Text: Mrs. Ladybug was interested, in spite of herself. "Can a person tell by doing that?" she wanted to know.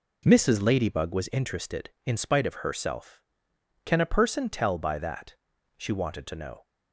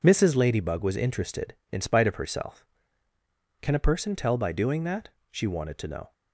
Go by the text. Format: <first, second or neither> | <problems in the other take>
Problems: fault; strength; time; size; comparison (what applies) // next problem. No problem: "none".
second | skips "doing"; at 4.9 s